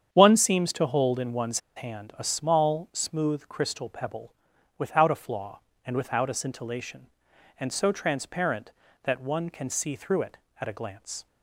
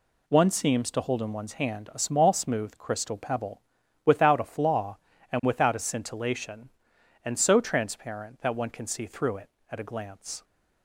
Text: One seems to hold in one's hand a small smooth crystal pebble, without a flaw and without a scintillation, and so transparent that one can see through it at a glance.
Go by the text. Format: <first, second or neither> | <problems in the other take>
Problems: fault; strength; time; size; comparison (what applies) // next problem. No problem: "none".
second | starts louder than the rest; strong; until 1.1 s; 8 dB // pauses between "one's" and "hand"; slight; at 1.5 s; 0.17 s long